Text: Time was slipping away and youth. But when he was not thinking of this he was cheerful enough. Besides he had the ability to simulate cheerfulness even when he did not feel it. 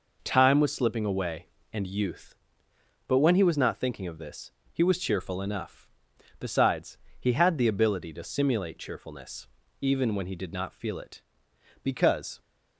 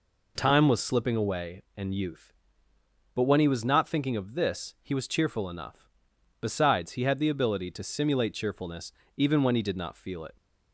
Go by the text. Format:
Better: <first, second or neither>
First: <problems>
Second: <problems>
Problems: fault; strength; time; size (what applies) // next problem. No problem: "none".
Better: second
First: pauses between "this" and "he"; slight; at 4.5 s; 0.22 s long // pauses between "Besides" and "he"; slight; at 6.9 s; 0.22 s long // pauses between "cheerfulness" and "even"; slight; at 9.4 s; 0.34 s long // goes on to say "Because"; from 11.8 s on; 0.58 s long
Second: pauses between "cheerfulness" and "even"; slight; at 8.9 s; 0.24 s long